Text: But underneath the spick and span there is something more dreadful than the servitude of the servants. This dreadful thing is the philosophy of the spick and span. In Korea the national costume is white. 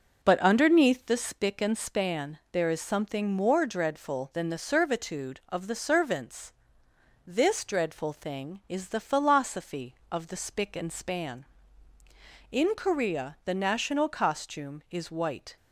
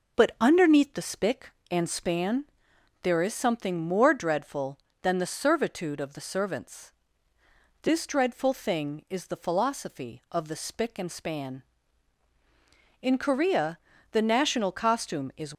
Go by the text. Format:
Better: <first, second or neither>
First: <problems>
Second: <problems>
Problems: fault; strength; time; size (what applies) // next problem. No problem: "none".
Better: first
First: none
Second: pauses between "span" and "there"; noticeable; at 2.4 s; 0.58 s long // pauses between "Korea" and "the"; slight; at 13.7 s; 0.36 s long // stops before "white"; at 15.5 s